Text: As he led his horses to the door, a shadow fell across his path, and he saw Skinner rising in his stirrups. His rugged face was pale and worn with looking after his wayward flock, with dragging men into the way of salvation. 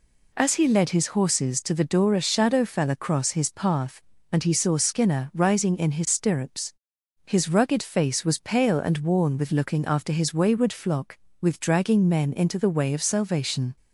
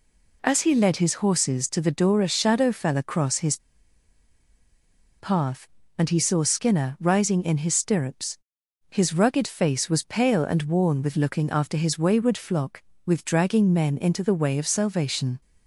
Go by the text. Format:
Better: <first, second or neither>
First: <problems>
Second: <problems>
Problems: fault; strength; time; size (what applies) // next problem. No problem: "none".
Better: first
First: none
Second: pauses between "his" and "path"; strong; at 3.5 s; 1.6 s long